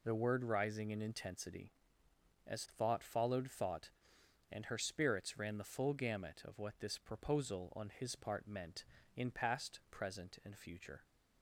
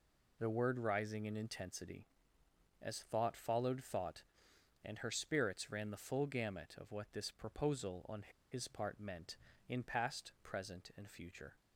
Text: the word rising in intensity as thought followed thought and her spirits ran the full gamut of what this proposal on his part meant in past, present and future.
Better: first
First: none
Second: pauses between "on" and "his"; slight; at 8.2 s; 0.27 s long

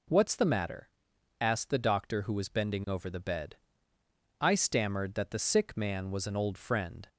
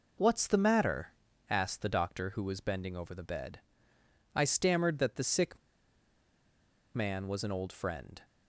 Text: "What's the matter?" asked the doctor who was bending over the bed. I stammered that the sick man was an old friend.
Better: first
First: none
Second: pauses between "sick" and "man"; strong; at 5.5 s; 1.3 s long

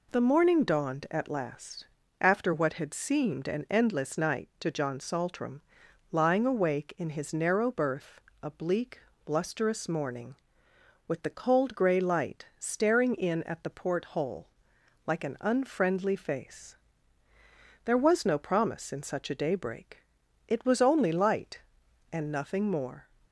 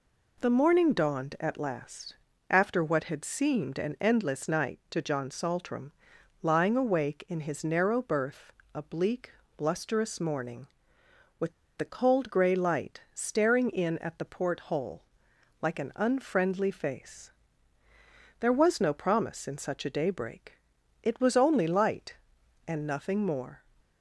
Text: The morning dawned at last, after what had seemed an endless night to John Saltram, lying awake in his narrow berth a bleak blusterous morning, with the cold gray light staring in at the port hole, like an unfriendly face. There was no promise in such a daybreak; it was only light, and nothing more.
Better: first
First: pauses between "berth" and "a"; slight; at 8.2 s; 0.20 s long // pauses between "bleak" and "blusterous"; slight; at 9.0 s; 0.24 s long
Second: pauses between "berth" and "a"; slight; at 8.5 s; 0.20 s long // pauses between "bleak" and "blusterous"; slight; at 9.3 s; 0.24 s long // pauses between "with" and "the"; slight; at 11.5 s; 0.25 s long

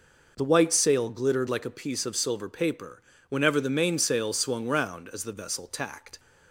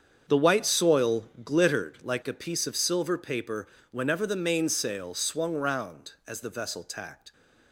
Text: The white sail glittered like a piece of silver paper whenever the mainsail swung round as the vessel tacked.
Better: first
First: pauses between "paper" and "whenever"; slight; at 3.0 s; 0.28 s long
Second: starts louder than the rest; strong; until 1.2 s; 7.5 dB // says "soil" for "sail"; at 0.6 s // pauses between "paper" and "whenever"; slight; at 3.6 s; 0.24 s long

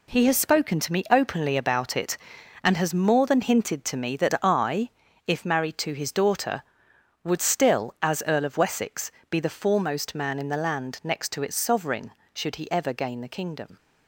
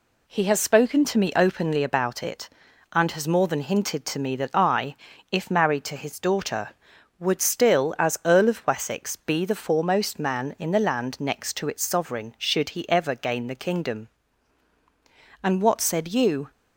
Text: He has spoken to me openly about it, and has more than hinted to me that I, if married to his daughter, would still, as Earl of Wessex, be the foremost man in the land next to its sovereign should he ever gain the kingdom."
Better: first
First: none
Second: goes on to say "And what said you"; noticeable; from 15.4 s on; 1.0 s long

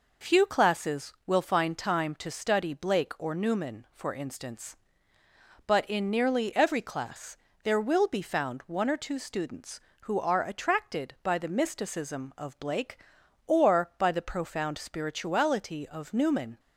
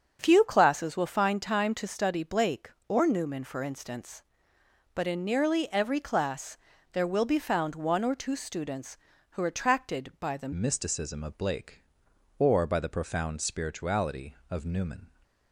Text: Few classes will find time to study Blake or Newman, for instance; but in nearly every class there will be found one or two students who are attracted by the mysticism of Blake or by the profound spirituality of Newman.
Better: first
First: pauses between "class" and "there"; slight; at 7.3 s; 0.28 s long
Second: starts louder than the rest; until 1.2 s; 7 dB // pauses between "class" and "there"; slight; at 6.5 s; 0.34 s long // changes voice at "mysticism"; from 10.5 s on; 4.5 s long

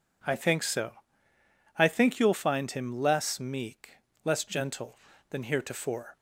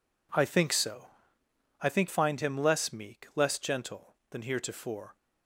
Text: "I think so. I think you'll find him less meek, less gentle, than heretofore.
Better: first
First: none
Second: skips "you'll"; at 2.0 s

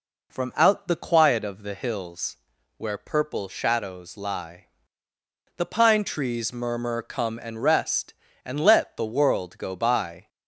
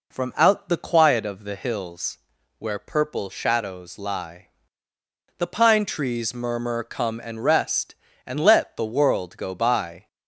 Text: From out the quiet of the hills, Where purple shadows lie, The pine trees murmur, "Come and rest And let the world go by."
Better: neither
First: none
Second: none

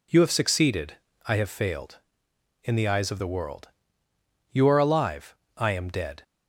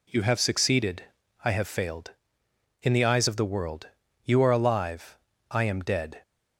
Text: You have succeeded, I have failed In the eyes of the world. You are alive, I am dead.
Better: neither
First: none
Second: none

